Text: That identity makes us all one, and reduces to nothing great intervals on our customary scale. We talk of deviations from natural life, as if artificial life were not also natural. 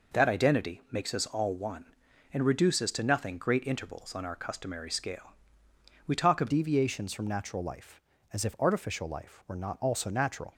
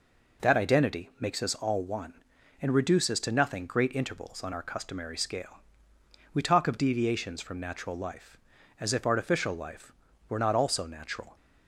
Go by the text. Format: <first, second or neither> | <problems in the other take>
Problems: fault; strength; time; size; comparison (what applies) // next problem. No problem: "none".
second | changes voice at "deviations"; from 6.4 s on; 4.1 s long